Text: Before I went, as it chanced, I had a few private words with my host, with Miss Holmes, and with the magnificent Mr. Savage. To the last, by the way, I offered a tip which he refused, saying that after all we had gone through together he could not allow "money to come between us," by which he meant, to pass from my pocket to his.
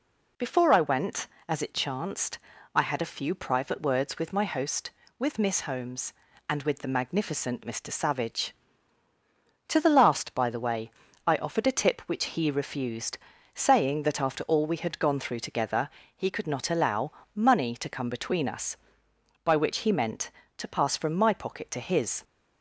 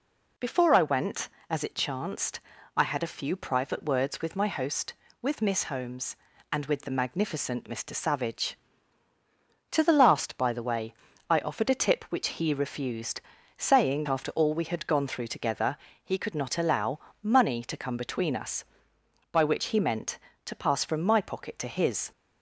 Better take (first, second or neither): first